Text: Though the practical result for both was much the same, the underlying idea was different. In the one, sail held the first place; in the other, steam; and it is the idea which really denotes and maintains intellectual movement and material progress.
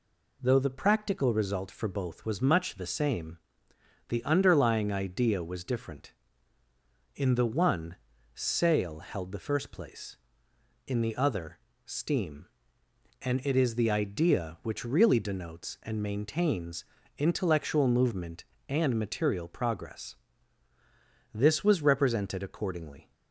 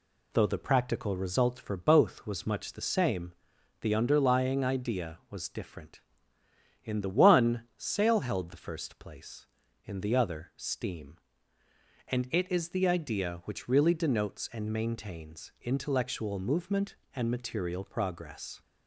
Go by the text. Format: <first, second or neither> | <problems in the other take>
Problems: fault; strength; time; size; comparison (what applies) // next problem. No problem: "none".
second | pauses between "maintains" and "intellectual"; slight; at 16.8 s; 0.34 s long // goes on to say "This was represented accordingly"; strong; from 21.3 s on; 1.7 s long